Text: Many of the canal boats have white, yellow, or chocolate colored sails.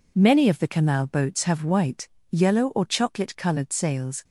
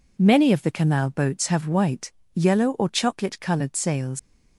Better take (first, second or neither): first